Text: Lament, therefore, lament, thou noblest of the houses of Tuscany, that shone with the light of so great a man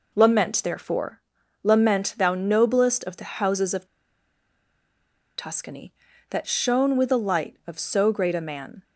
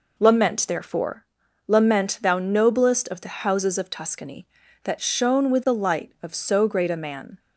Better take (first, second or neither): second